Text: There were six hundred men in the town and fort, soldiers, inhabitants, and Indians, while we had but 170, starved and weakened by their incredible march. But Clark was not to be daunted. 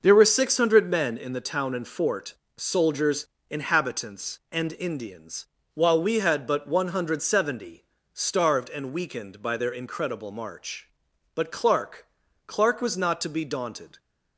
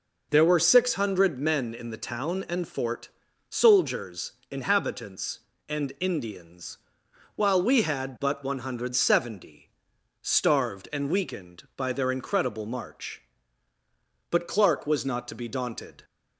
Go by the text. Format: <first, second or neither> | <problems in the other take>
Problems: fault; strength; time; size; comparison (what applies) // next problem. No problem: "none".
second | says "Clark" twice; at 12.4 s